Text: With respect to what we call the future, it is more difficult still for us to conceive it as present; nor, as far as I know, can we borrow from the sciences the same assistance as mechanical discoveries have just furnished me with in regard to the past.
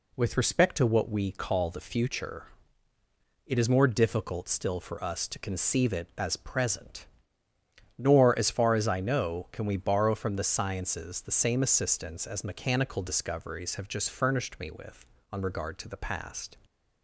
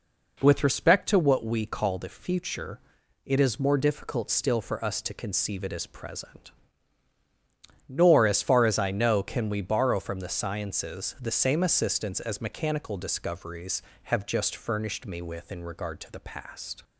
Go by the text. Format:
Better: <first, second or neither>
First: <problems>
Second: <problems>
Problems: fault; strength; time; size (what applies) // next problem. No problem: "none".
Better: second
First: says "on" for "in"; at 15.3 s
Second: none